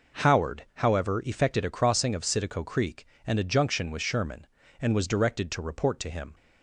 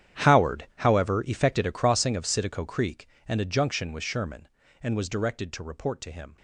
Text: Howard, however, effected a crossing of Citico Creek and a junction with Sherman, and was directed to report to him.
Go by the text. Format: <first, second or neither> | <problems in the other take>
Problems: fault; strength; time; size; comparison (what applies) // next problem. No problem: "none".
first | gets quieter; strong; throughout; 18 dB